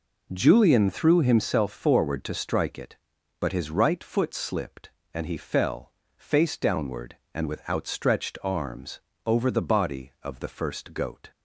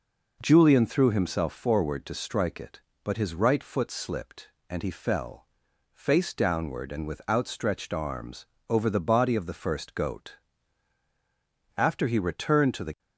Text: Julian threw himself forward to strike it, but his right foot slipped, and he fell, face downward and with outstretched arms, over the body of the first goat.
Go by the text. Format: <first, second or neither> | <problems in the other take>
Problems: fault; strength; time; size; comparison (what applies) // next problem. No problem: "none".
first | goes on to say "After he returned to the"; noticeable; from 11.7 s on; 1.2 s long